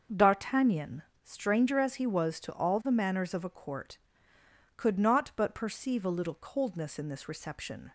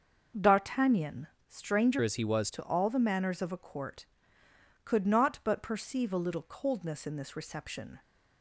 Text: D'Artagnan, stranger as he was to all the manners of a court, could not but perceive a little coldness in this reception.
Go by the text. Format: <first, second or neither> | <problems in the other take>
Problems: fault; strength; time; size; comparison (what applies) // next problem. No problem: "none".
first | starts louder than the rest; noticeable; until 1.5 s; 6 dB; also in the first // changes voice from "as" to "was"; from 2.0 to 2.4 s; 0.4 s long